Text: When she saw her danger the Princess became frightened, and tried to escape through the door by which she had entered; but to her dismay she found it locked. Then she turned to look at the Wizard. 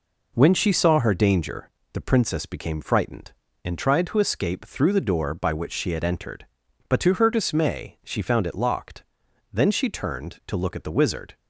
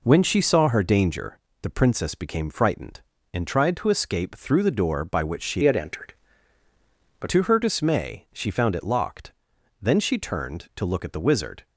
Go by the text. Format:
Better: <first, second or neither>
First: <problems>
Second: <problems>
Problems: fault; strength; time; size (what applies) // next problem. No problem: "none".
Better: first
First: pauses between "danger" and "the"; slight; at 1.7 s; 0.22 s long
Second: pauses between "danger" and "the"; slight; at 1.3 s; 0.22 s long // changes voice from "had" to "but"; from 5.6 to 7.2 s; 1.6 s long